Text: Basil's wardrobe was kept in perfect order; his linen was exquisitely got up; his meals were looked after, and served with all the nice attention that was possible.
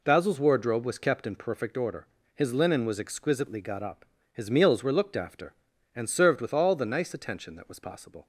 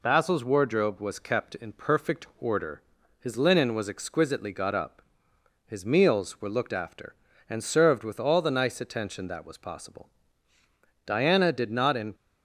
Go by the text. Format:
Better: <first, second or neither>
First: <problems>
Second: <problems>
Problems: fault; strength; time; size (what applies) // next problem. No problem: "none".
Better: first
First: none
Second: goes on to say "Diana did not in"; noticeable; from 11.0 s on; 1.1 s long